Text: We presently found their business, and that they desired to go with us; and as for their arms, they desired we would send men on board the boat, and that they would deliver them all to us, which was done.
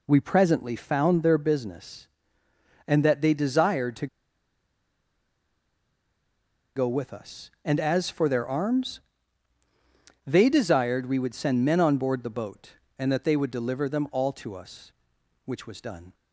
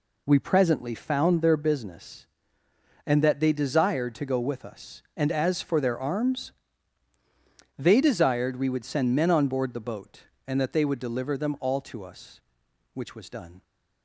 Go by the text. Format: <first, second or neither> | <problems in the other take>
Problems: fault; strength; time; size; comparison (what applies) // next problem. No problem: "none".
second | pauses between "to" and "go"; strong; at 4.0 s; 2.6 s long